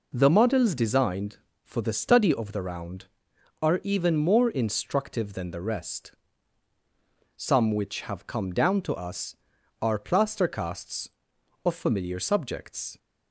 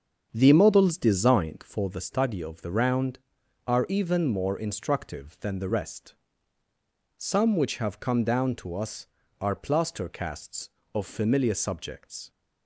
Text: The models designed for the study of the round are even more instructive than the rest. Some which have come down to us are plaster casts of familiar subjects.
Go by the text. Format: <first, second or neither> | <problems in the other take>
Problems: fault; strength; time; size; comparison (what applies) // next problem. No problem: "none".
first | starts louder than the rest; strong; until 2.0 s; 7.5 dB